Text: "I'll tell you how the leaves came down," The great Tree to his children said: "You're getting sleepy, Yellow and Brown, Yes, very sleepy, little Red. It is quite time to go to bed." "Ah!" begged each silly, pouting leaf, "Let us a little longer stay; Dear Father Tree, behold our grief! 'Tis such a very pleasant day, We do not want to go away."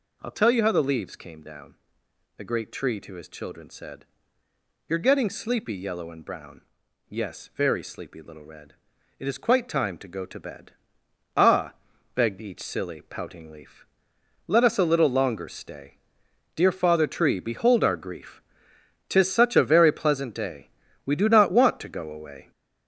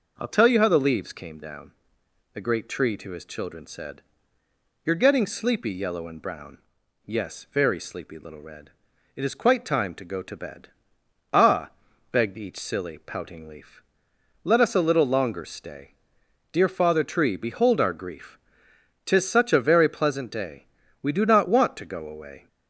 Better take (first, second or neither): second